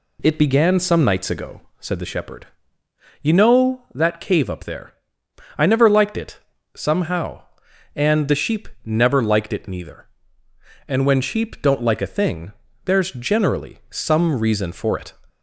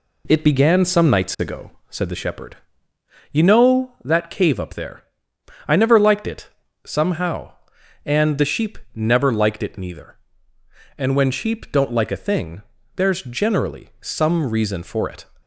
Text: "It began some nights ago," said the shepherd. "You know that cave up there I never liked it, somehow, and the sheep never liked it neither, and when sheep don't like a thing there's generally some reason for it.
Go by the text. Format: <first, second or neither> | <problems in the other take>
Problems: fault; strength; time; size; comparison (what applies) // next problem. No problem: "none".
first | gets quieter; throughout; 4 dB // pauses between "there" and "I"; noticeable; at 5.0 s; 0.64 s long; noticeable in the first // pauses between "sheep" and "never"; slight; at 8.7 s; 0.16 s long; slight in the first // pauses between "thing" and "there's"; slight; at 12.6 s; 0.32 s long; slight in the first